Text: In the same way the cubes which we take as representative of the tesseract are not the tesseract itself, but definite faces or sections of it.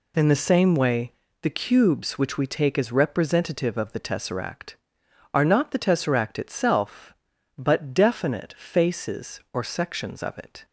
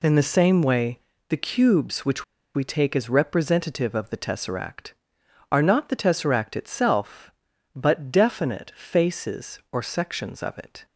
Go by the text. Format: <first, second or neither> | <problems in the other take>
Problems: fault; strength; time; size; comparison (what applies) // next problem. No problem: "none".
first | pauses between "way" and "the"; slight; at 0.9 s; 0.30 s long; slight in the first // pauses between "which" and "we"; slight; at 2.2 s; 0.30 s long